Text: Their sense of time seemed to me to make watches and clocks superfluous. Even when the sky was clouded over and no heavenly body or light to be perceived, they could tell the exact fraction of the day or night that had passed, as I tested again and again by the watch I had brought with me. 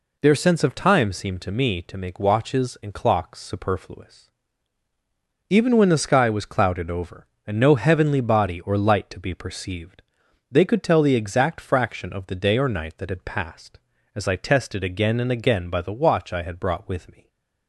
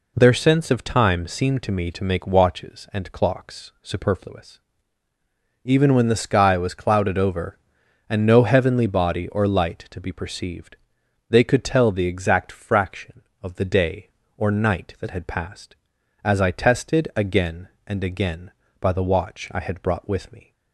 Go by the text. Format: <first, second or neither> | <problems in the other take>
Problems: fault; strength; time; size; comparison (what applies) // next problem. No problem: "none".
neither | none